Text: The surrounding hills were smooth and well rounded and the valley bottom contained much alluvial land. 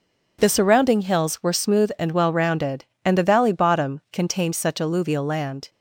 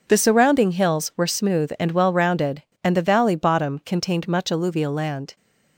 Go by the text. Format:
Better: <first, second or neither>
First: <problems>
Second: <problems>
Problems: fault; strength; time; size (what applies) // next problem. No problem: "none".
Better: second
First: says "such" for "much"; at 4.5 s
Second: none